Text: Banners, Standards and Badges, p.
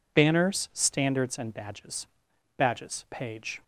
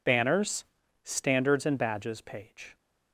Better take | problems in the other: second | says "Badges" twice; at 2.5 s

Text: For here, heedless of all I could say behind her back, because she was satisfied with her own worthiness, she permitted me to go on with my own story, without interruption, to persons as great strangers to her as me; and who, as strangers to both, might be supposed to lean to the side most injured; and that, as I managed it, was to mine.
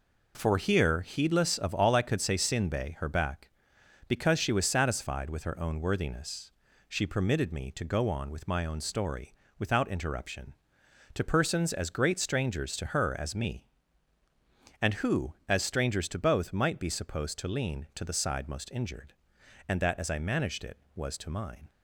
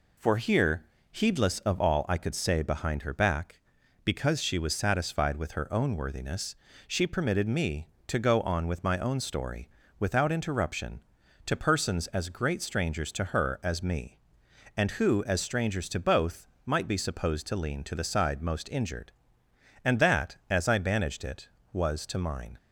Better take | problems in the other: second | says "sinbe" for "behind"; at 2.3 s

